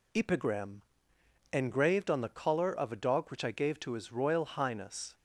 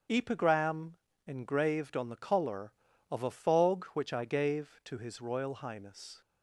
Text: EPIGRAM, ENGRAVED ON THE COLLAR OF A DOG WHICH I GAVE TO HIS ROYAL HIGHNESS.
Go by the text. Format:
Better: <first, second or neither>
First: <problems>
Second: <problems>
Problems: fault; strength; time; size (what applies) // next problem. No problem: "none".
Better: first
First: none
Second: starts louder than the rest; until 1.3 s; 7 dB // says "Fog" for "DOG"; at 3.3 s